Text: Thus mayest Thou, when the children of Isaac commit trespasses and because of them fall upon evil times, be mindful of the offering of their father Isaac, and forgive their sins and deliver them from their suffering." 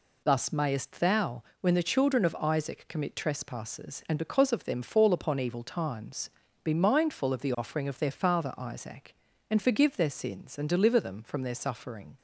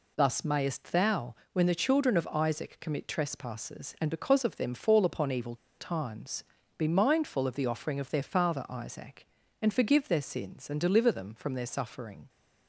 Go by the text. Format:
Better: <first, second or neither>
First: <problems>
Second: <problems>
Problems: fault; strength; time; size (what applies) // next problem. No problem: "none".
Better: first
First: none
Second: pauses between "evil" and "times"; slight; at 5.5 s; 0.24 s long